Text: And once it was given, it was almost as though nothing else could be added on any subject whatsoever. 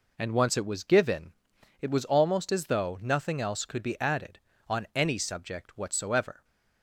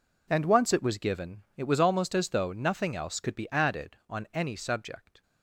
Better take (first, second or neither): first